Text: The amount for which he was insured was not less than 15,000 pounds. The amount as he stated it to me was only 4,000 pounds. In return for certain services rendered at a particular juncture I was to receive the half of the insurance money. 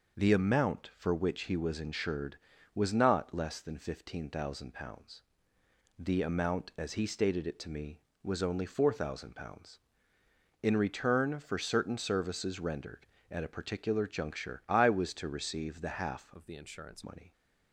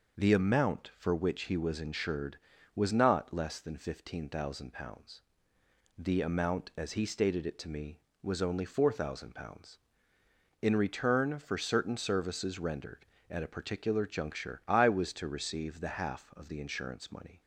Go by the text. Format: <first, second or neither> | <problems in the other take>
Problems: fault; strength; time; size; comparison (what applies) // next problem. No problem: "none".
second | changes voice from "of" to "insurance"; from 16.3 to 17.0 s; 0.7 s long